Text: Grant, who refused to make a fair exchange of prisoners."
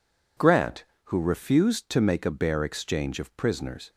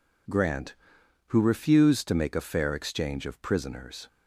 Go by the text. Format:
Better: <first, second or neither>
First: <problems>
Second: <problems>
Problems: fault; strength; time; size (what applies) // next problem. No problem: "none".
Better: second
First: says "bare" for "fair"; at 2.2 s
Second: none